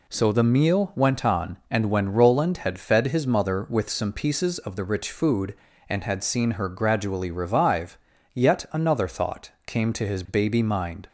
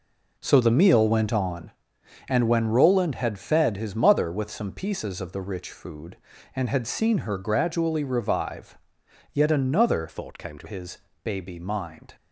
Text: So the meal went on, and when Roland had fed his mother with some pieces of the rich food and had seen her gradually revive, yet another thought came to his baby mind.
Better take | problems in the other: first | changes voice from "thought" to "to"; from 10.0 to 10.6 s; 0.6 s long // pauses between "his" and "baby"; slight; at 10.9 s; 0.26 s long

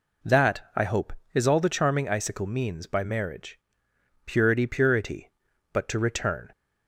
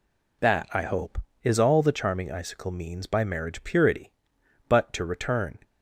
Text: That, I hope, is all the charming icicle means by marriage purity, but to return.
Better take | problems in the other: second | pauses between "marriage" and "purity"; noticeable; at 3.5 s; 0.68 s long // says "purity" twice; at 4.6 s

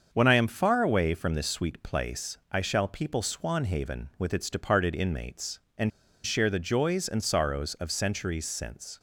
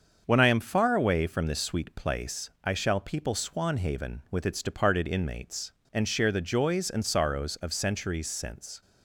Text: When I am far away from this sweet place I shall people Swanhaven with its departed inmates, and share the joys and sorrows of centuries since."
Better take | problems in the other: second | starts louder than the rest; until 1.1 s; 7 dB; also in the second // pauses between "place" and "I"; slight; at 2.3 s; 0.16 s long; slight in the second // pauses between "and" and "share"; slight; at 5.8 s; 0.34 s long

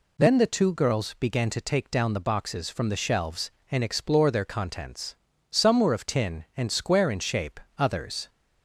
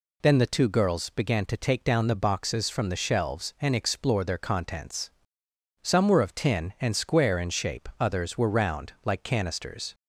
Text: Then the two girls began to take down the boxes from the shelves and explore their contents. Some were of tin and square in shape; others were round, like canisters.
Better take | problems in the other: second | stops before "were round like canisters"; at 8.2 s

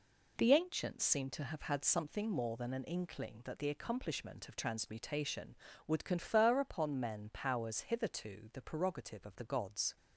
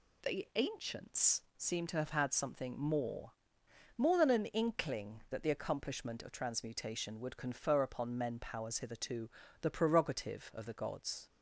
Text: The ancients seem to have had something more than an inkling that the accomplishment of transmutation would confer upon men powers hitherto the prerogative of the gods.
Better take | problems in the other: first | says "more" twice; at 3.9 s // pauses between "hitherto" and "the"; slight; at 9.2 s; 0.32 s long

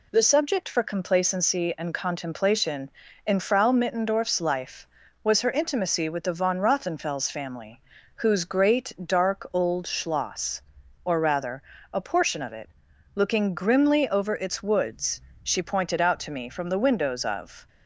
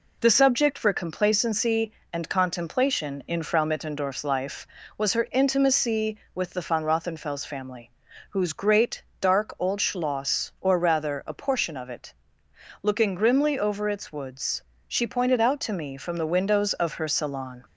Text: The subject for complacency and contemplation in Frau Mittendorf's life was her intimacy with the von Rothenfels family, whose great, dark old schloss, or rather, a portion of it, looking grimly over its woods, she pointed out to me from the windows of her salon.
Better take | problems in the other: second | stops before "her salon"; at 17.6 s

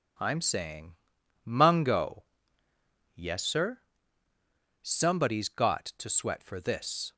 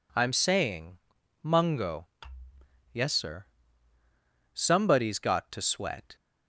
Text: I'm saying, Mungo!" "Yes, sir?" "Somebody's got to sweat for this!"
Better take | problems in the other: first | stops before "for this"; at 6.1 s

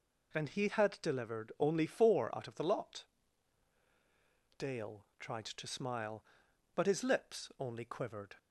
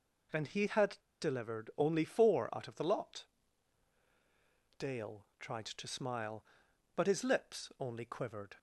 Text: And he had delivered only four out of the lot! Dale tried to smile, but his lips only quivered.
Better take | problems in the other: first | pauses between "had" and "delivered"; slight; at 0.9 s; 0.23 s long

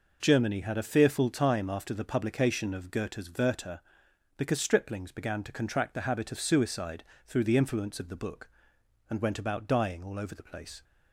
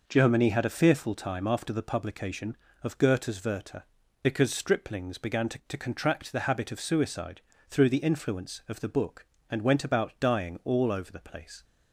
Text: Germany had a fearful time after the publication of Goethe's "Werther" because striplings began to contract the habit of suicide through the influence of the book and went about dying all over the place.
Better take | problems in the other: first | says "to" twice; at 5.6 s // pauses between "suicide" and "through"; slight; at 7.4 s; 0.28 s long; slight in the first

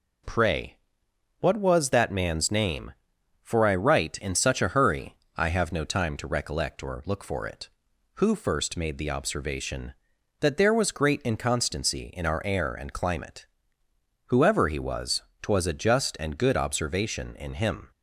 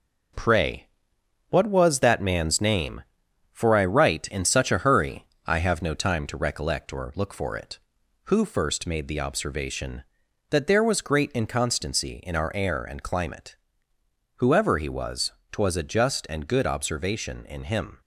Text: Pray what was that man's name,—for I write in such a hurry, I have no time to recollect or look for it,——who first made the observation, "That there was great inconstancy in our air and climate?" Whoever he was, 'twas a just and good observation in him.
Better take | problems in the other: first | gets quieter; noticeable; throughout; 5 dB // pauses between "Pray" and "what"; noticeable; at 0.8 s; 0.64 s long; noticeable in the first

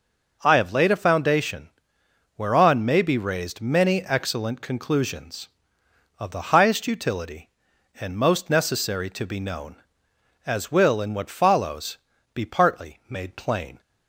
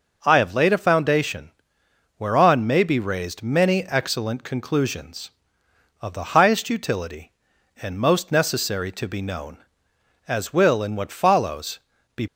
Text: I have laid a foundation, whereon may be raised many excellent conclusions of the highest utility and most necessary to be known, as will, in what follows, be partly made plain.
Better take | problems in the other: first | stops before "partly made plain"; at 12.2 s

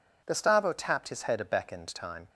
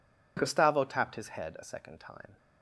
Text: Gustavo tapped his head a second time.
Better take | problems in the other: second | says "beckoned" for "second"; at 1.4 s

